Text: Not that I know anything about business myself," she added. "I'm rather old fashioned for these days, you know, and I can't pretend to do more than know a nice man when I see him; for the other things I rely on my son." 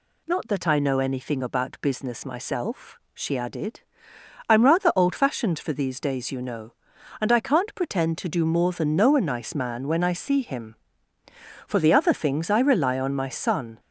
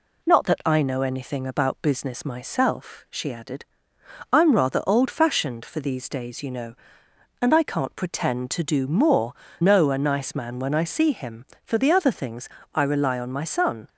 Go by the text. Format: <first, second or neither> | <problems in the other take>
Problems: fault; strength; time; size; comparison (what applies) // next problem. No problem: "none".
first | skips "than"; at 9.4 s // pauses between "things" and "I"; slight; at 12.4 s; 0.26 s long